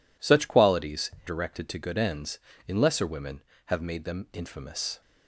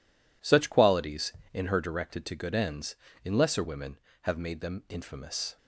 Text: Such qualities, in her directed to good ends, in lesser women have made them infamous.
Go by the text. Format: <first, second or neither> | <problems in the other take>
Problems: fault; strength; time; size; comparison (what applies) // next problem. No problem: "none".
second | skips "in her"; at 1.1 s